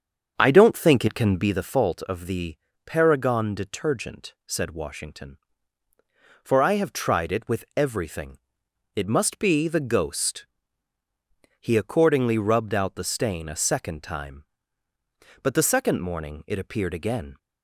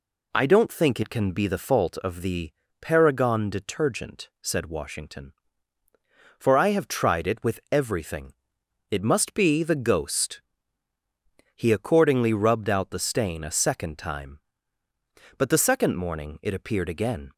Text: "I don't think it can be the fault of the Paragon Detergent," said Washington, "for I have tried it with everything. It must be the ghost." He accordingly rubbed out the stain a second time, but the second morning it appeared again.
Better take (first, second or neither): second